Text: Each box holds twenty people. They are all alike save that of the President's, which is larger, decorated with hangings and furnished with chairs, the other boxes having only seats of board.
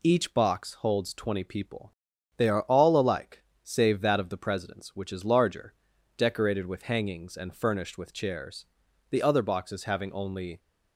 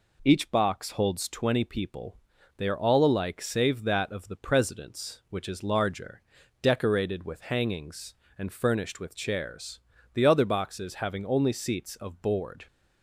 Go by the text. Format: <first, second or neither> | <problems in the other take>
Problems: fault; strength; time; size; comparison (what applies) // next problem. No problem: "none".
second | pauses between "alike" and "save"; slight; at 3.4 s; 0.20 s long // stops before "seats of board"; at 10.5 s